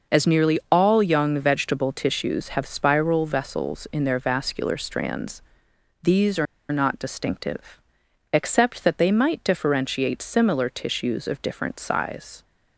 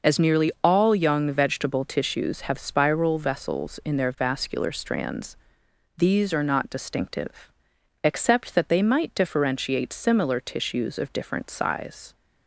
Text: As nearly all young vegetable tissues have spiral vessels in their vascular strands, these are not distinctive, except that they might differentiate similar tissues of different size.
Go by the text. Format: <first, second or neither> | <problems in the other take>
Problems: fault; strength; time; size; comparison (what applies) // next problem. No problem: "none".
second | pauses between "are" and "not"; slight; at 6.4 s; 0.26 s long